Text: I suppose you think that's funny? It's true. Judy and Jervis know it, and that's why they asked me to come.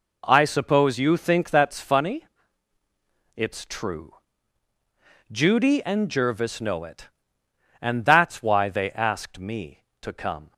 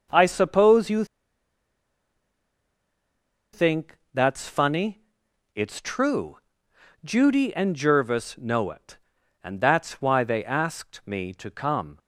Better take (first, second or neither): first